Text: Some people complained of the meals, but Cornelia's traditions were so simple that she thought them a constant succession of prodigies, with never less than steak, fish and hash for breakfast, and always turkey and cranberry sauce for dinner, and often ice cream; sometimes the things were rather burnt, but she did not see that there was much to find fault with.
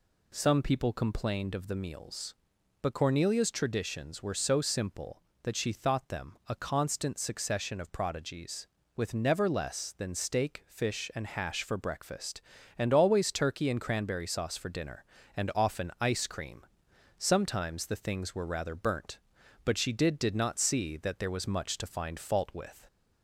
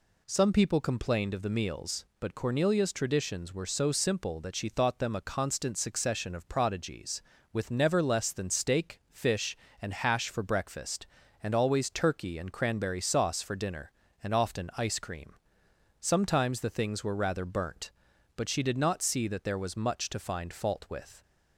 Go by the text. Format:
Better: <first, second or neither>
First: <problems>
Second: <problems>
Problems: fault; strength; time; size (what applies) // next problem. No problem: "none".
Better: second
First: says "did" twice; at 20.1 s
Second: none